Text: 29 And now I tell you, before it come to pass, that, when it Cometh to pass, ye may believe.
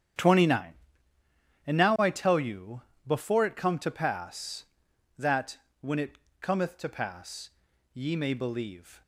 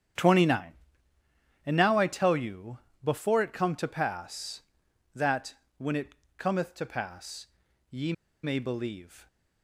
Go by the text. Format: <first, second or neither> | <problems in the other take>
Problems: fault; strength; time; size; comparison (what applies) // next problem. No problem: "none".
first | starts louder than the rest; strong; until 2.1 s; 9.5 dB; strong in the first // pauses between "it" and "Cometh"; slight; at 6.1 s; 0.26 s long; slight in the first // pauses between "ye" and "may"; slight; at 8.1 s; 0.31 s long